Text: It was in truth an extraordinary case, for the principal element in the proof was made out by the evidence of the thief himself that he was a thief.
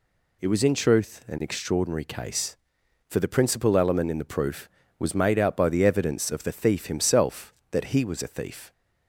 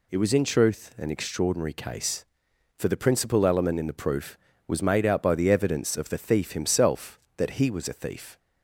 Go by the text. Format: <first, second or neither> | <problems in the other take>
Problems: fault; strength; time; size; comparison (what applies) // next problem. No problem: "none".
neither | none